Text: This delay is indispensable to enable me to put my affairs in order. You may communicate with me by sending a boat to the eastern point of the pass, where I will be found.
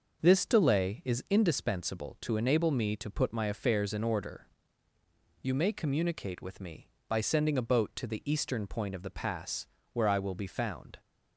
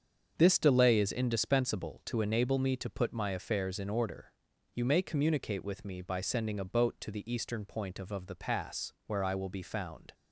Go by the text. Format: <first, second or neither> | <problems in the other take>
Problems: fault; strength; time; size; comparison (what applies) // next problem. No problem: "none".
first | starts louder than the rest; strong; until 1.3 s; 7 dB // says "of" twice; at 8.0 s